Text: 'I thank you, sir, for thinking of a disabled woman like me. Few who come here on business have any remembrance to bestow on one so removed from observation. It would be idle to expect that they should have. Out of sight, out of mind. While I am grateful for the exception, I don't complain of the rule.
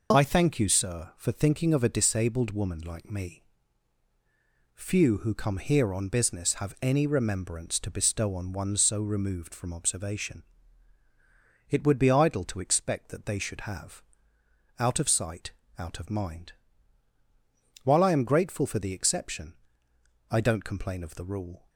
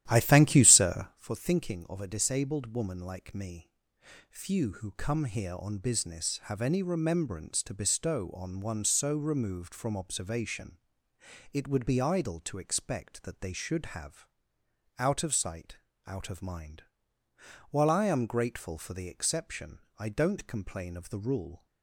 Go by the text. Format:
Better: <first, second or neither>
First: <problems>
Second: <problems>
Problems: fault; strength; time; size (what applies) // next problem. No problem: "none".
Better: first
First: none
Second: starts louder than the rest; strong; until 1.3 s; 12.5 dB